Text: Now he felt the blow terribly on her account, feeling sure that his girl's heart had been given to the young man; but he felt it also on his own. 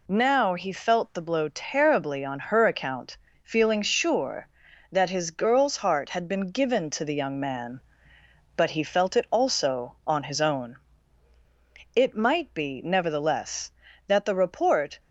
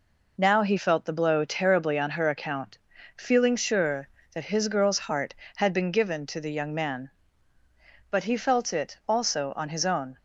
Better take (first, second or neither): second